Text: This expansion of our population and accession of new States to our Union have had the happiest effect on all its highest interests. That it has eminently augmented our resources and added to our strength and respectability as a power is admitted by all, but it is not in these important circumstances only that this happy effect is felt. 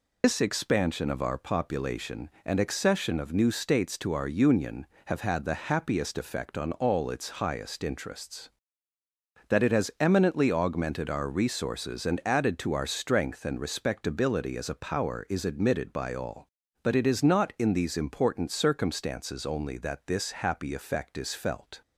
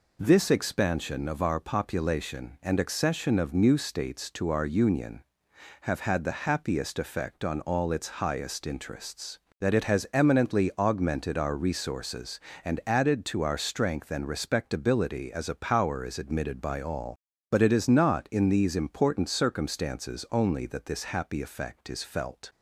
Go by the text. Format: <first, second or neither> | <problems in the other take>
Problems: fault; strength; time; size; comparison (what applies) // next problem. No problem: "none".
second | loses the start of "This"; at 0.2 s; 150 ms